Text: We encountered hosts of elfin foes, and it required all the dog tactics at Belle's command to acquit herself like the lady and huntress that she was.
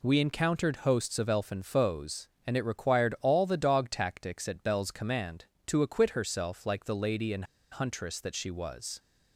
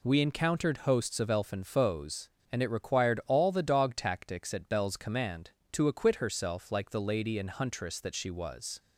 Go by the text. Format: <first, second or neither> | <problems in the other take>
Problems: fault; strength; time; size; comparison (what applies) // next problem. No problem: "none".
second | pauses between "and" and "huntress"; slight; at 7.4 s; 0.27 s long